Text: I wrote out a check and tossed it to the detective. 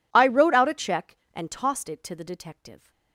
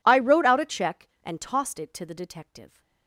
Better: neither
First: none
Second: none

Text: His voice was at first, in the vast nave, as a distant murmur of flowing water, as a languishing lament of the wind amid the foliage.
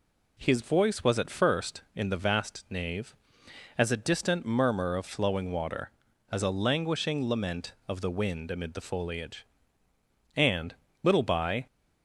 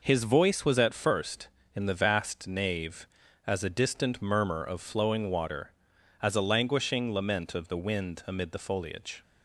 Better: second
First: goes on to say "And little by"; noticeable; from 10.3 s on; 1.3 s long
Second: none

